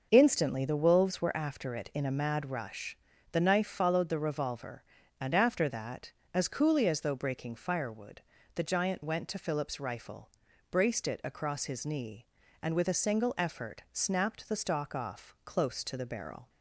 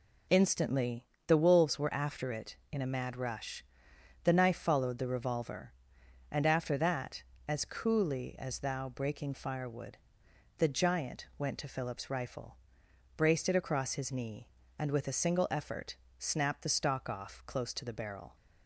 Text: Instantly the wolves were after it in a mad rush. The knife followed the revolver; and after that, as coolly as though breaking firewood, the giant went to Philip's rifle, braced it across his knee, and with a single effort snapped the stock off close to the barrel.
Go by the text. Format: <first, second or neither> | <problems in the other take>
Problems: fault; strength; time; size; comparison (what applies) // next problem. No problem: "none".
first | pauses between "Instantly" and "the"; slight; at 1.0 s; 0.22 s long // says "thou" for "though"; at 8.5 s // pauses between "effort" and "snapped"; slight; at 15.9 s; 0.22 s long